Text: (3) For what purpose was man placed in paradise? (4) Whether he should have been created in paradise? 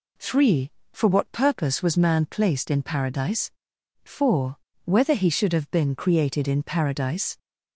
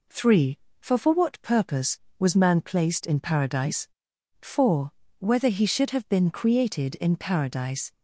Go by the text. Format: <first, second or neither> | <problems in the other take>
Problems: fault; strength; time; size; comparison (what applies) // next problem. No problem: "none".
first | says "For" twice; at 0.9 s